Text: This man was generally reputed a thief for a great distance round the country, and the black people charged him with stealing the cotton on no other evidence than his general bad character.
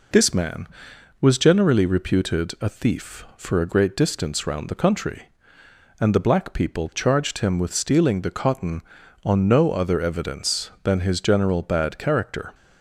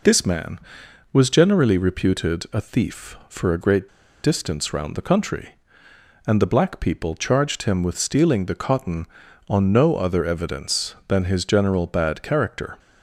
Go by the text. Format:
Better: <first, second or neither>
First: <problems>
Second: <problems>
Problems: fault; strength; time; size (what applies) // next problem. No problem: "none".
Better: first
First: none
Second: pauses between "great" and "distance"; slight; at 3.8 s; 0.35 s long